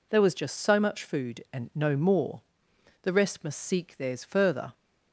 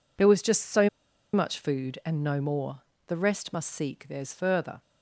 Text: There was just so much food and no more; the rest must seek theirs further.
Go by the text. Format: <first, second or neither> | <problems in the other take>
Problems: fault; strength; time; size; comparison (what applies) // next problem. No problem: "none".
first | pauses between "so" and "much"; at 0.8 s; 0.45 s long